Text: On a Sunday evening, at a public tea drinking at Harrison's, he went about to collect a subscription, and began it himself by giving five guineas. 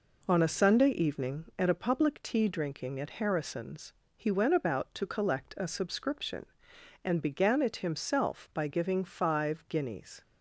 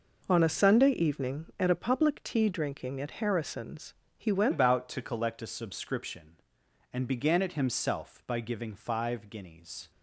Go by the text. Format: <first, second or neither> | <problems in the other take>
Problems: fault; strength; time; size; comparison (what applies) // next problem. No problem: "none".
first | changes voice at "about"; from 4.5 s on; 5.4 s long